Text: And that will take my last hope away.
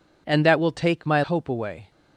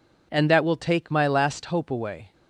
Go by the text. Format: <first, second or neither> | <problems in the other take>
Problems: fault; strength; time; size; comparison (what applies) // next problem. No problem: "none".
second | skips "last"; at 1.2 s